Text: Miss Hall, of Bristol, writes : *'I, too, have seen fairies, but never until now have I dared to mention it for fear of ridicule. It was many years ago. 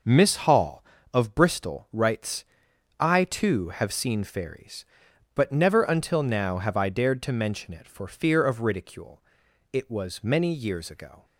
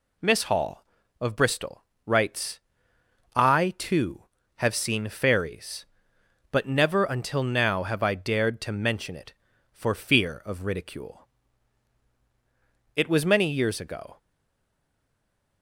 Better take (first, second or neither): first